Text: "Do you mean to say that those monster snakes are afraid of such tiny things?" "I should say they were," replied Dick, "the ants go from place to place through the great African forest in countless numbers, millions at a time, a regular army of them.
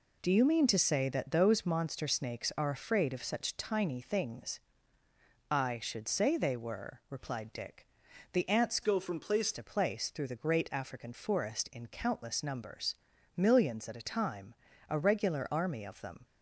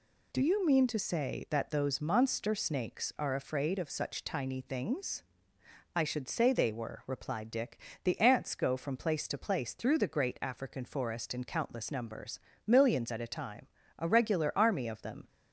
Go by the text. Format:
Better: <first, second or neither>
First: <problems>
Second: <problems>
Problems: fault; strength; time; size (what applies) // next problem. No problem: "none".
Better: second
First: changes voice from "go" to "place"; from 8.8 to 9.5 s; 0.7 s long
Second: none